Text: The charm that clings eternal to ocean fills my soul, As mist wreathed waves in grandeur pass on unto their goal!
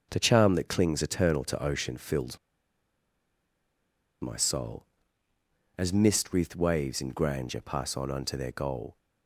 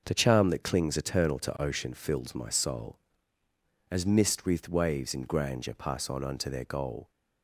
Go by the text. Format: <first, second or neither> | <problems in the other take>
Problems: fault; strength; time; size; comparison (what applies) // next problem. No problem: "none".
second | starts louder than the rest; noticeable; until 1.1 s; 6 dB; noticeable in the second // pauses between "fills" and "my"; strong; at 2.3 s; 1.8 s long